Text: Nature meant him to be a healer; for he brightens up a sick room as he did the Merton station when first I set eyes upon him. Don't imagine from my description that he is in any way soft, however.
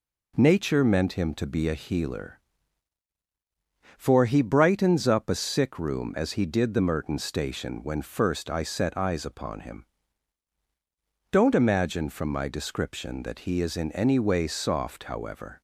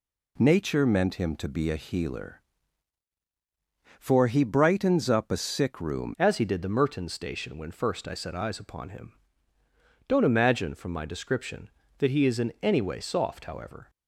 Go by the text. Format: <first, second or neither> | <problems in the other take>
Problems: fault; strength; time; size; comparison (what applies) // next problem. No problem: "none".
first | changes voice at "as"; from 6.1 s on; 7.7 s long